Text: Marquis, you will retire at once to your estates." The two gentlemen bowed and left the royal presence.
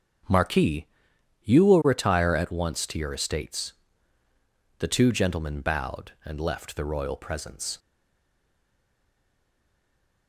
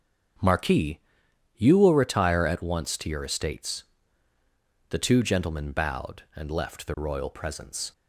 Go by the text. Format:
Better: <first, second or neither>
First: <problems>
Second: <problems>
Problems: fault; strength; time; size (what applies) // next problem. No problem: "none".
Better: second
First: starts louder than the rest; until 1.8 s; 7 dB // stays silent after the last word; from 7.7 s on; 2.5 s long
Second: starts louder than the rest; until 1.9 s; 7 dB